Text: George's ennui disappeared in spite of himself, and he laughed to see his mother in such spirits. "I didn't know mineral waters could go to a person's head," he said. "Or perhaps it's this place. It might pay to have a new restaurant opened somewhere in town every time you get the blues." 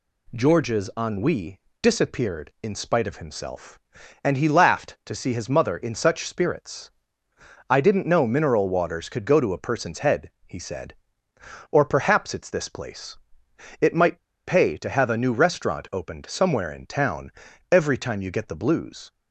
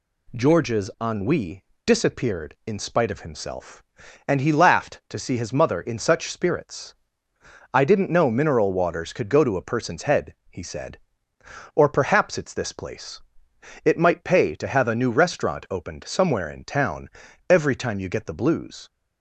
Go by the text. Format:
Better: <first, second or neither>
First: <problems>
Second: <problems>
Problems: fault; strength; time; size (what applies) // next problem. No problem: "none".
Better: second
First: pauses between "ennui" and "disappeared"; slight; at 1.5 s; 0.22 s long // pauses between "might" and "pay"; slight; at 14.1 s; 0.26 s long // pauses between "town" and "every"; at 17.3 s; 0.40 s long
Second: pauses between "ennui" and "disappeared"; slight; at 1.6 s; 0.22 s long // pauses between "town" and "every"; at 17.0 s; 0.40 s long